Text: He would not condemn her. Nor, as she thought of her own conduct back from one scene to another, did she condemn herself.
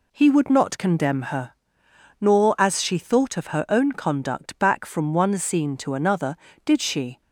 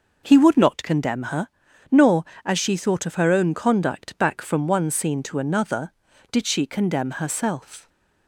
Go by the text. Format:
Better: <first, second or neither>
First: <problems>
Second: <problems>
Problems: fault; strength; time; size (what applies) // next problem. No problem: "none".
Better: second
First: stops before "condemn herself"; at 7.2 s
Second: none